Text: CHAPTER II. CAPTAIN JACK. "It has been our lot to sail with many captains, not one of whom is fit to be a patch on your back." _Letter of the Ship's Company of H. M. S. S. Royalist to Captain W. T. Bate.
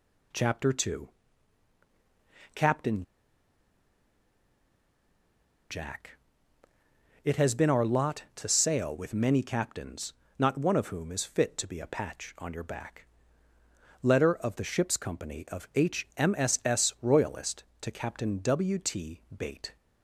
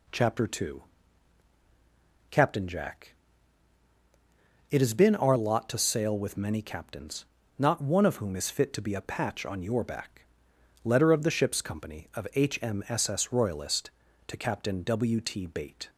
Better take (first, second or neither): second